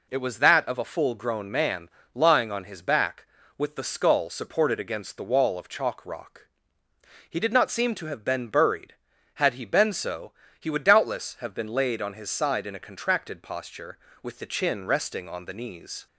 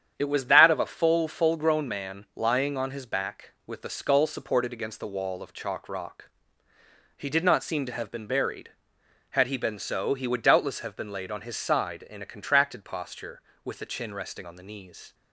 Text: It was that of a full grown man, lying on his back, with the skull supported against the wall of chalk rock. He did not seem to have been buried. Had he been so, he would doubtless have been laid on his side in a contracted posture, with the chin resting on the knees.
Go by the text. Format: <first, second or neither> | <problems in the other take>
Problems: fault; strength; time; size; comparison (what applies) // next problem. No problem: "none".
first | starts louder than the rest; strong; until 1.1 s; 9 dB // says "full" twice; at 1.2 s